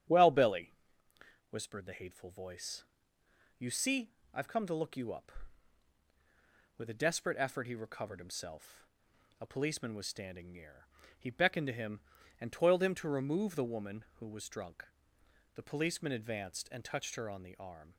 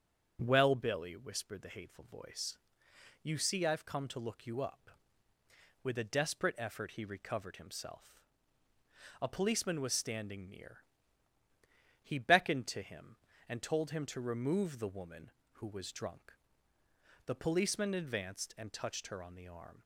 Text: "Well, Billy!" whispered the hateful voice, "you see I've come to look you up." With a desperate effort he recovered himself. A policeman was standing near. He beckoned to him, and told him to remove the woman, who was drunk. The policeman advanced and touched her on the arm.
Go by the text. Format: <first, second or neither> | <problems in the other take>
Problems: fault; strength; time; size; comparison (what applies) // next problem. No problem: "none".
second | starts louder than the rest; strong; until 1.8 s; 10 dB; strong in the second // pauses between "see" and "I've"; slight; at 4.1 s; 0.20 s long // says "toiled" for "told"; at 12.5 s